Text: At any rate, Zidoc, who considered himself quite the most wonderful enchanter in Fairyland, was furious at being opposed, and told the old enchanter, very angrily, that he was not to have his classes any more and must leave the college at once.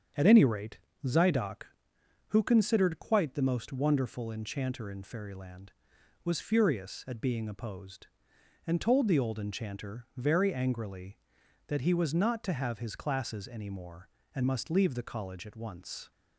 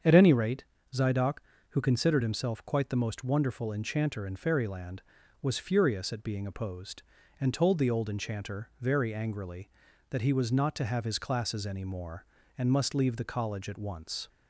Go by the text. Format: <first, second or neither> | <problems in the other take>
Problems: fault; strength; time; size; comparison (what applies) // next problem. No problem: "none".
second | starts louder than the rest; strong; until 1.4 s; 7.5 dB; strong in the second // skips "himself"; at 2.9 s